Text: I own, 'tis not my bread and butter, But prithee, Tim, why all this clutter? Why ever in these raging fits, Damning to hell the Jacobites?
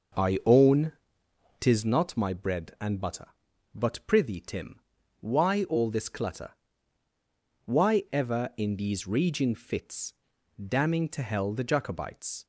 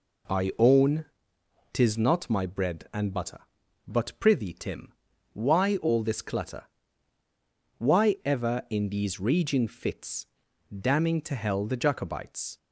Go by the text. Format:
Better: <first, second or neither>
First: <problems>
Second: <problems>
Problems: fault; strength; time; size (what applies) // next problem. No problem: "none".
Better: second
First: starts louder than the rest; noticeable; until 1.9 s; 5.5 dB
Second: none